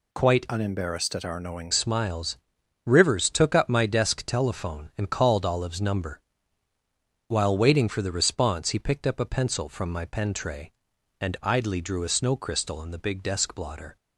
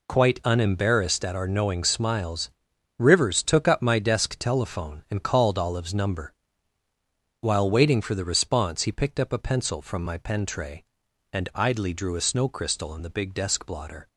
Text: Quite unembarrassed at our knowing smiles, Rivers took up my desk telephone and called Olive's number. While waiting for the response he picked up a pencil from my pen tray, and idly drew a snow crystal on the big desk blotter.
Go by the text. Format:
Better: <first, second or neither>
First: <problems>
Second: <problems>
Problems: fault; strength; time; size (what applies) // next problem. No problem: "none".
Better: second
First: changes voice from "unembarrassed" to "knowing"; from 0.4 to 1.7 s; 1.3 s long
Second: none